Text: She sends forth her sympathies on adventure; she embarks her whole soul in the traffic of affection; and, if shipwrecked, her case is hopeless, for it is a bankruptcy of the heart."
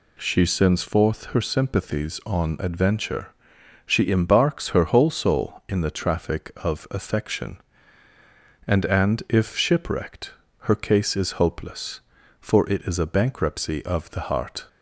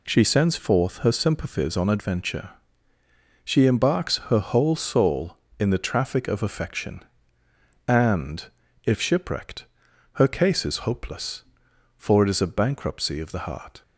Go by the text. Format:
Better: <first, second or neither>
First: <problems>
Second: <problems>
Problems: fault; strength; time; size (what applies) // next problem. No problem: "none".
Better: second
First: says "and" twice; at 8.8 s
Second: none